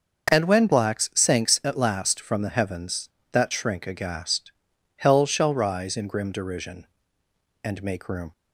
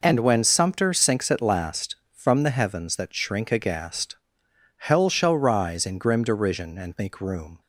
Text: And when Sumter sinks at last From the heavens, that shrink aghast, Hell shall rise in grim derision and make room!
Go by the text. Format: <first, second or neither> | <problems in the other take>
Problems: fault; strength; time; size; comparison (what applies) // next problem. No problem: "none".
second | starts louder than the rest; until 1.3 s; 6.5 dB // says "Blacks" for "Sumter"; at 0.6 s